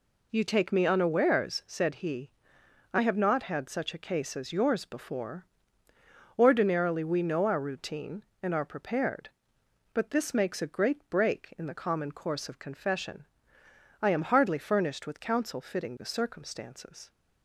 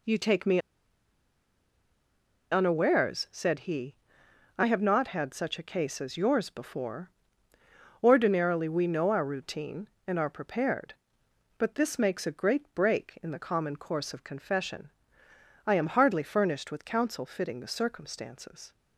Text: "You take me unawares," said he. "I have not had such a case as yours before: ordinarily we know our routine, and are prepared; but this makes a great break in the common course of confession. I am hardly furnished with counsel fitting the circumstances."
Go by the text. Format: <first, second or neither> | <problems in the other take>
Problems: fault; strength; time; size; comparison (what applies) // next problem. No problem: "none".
first | pauses between "me" and "unawares"; strong; at 0.5 s; 1.9 s long